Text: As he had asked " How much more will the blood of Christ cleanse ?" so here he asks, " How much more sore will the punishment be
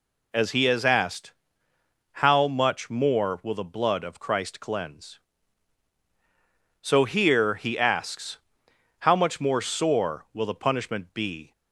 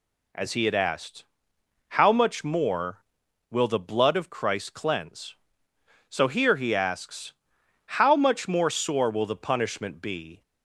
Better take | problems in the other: second | says "has" for "had"; at 0.6 s

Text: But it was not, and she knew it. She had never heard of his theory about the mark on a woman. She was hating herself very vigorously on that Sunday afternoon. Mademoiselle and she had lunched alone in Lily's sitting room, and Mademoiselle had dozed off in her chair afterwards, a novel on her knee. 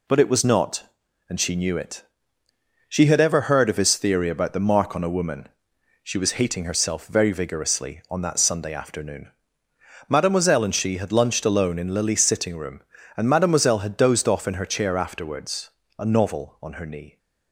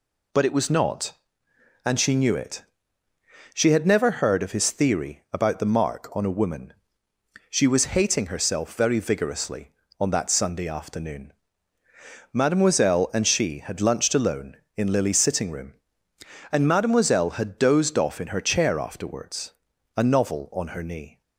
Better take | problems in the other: second | says "ever" for "never"; at 3.1 s

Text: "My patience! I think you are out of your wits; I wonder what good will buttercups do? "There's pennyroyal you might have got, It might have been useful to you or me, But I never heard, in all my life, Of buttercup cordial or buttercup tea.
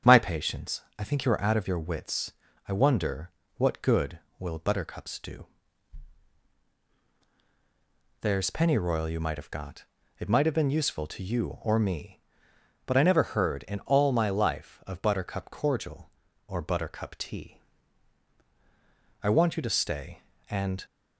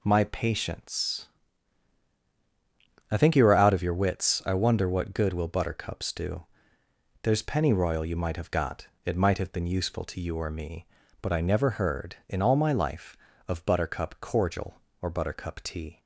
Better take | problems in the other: second | starts louder than the rest; strong; until 1.2 s; 8 dB // pauses between "wonder" and "what"; slight; at 3.3 s; 0.26 s long // goes on to say "I want you to stay and"; from 19.2 s on; 1.6 s long

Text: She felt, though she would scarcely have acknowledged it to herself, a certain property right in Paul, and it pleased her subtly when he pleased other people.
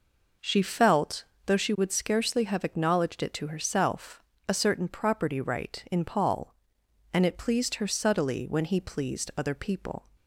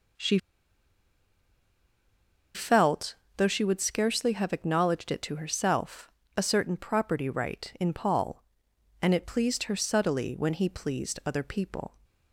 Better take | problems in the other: first | pauses between "She" and "felt"; strong; at 0.3 s; 2.1 s long

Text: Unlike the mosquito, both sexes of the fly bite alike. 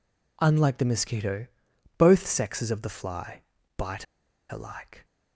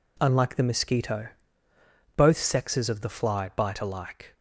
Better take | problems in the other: second | pauses between "fly" and "bite"; at 3.3 s; 0.38 s long // pauses between "bite" and "alike"; at 4.0 s; 0.45 s long

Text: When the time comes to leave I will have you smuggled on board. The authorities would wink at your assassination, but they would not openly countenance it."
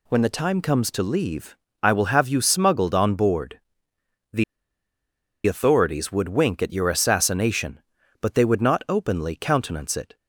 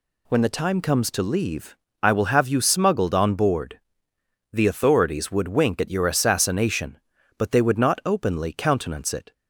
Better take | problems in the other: second | pauses between "leave" and "I"; slight; at 1.5 s; 0.26 s long; slight in the second // pauses between "The" and "authorities"; at 4.4 s; 1.0 s long

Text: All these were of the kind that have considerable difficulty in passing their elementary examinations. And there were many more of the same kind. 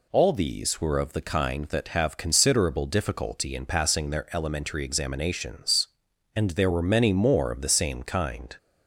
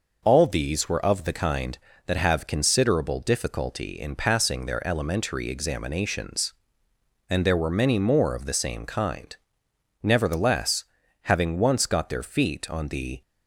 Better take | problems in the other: first | goes on to say "Nevertheless having once got their feet on the"; strong; from 10.0 s on; 3.1 s long

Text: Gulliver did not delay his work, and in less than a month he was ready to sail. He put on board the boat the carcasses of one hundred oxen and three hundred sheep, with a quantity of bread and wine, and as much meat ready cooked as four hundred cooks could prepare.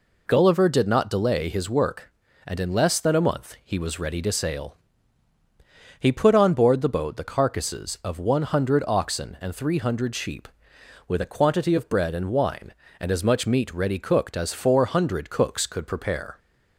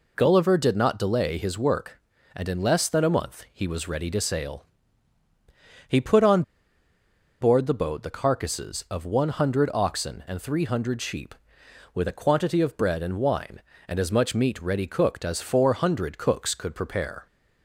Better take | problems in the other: first | pauses between "on" and "board"; at 6.4 s; 0.99 s long

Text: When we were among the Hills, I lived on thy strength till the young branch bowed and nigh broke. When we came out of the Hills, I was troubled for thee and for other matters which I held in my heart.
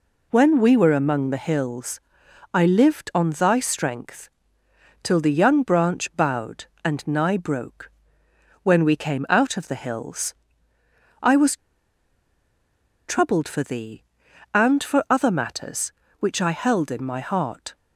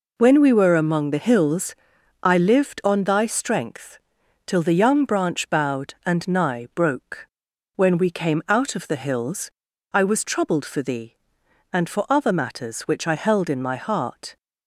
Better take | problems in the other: second | pauses between "strength" and "till"; noticeable; at 4.2 s; 0.74 s long; noticeable in the second // pauses between "was" and "troubled"; strong; at 11.5 s; 1.5 s long

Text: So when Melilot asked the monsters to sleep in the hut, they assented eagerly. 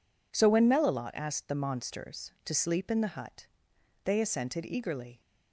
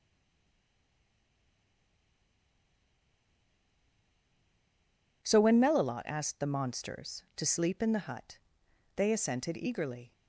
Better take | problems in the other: first | stays silent before the first word; strong; until 5.2 s; 5.2 s long

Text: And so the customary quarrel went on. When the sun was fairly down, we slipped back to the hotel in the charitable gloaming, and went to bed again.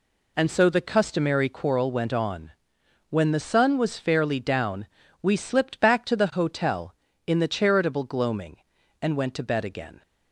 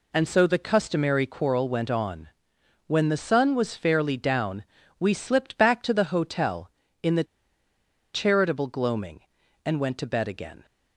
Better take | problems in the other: first | pauses between "the" and "charitable"; noticeable; at 7.2 s; 0.90 s long

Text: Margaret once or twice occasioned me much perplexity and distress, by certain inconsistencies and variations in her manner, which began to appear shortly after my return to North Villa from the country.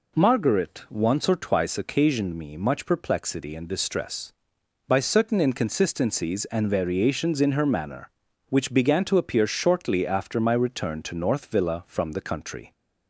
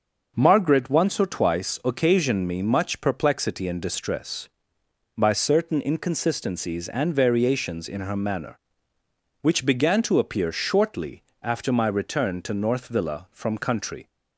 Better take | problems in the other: first | pauses between "shortly" and "after"; slight; at 11.2 s; 0.18 s long // skips "the"; at 13.5 s

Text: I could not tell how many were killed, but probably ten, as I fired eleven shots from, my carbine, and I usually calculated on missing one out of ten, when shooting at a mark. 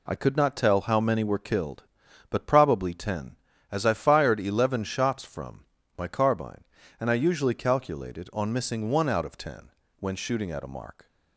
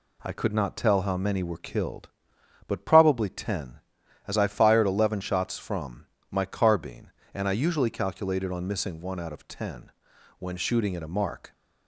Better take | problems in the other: neither | none

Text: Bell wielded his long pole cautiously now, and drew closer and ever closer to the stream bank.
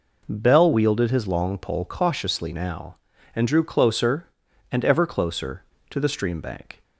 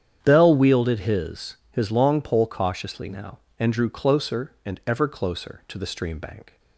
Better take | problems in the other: first | starts louder than the rest; strong; until 1.2 s; 8.5 dB // says "his" twice; at 1.7 s

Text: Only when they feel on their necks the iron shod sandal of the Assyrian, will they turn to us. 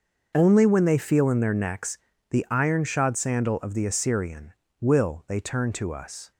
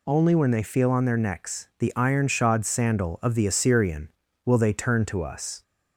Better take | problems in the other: second | starts louder than the rest; until 1.3 s; 6 dB // says "in" for "on"; at 1.3 s // pauses between "necks" and "the"; slight; at 1.9 s; 0.32 s long

